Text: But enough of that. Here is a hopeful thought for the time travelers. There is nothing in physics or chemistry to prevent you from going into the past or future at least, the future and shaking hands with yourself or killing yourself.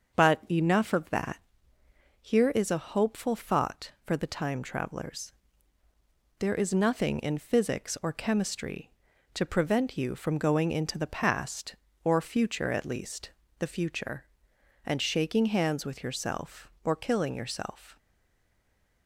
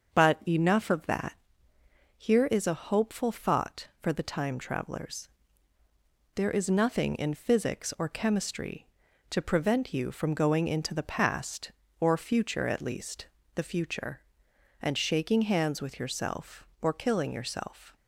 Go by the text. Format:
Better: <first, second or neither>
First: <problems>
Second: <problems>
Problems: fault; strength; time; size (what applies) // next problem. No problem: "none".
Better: second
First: starts louder than the rest; until 1.2 s; 6.5 dB // stays silent after the last word; from 17.9 s on; 1.1 s long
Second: starts louder than the rest; until 1.2 s; 6.5 dB